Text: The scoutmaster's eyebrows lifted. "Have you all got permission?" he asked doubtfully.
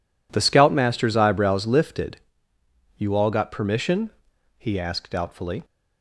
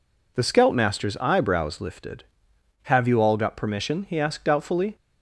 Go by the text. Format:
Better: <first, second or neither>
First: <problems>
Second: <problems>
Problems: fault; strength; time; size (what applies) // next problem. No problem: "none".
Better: second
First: skips "Have"; at 2.5 s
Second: none